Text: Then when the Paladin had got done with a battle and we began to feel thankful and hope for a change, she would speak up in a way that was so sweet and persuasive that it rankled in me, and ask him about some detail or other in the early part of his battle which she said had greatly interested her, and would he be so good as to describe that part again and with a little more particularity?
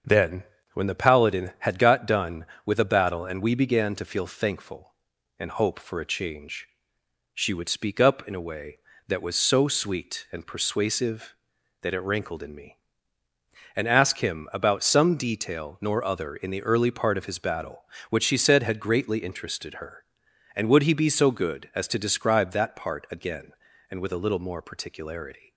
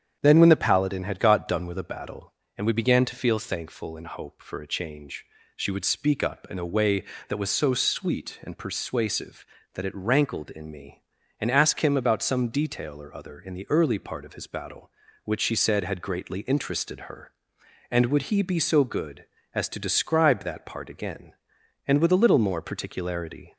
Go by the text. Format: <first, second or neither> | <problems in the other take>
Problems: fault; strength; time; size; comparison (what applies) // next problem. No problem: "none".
second | starts louder than the rest; until 1.3 s; 7 dB; strong in the second // pauses between "Then" and "when"; slight; at 0.4 s; 0.30 s long // says "nor" for "or"; at 15.7 s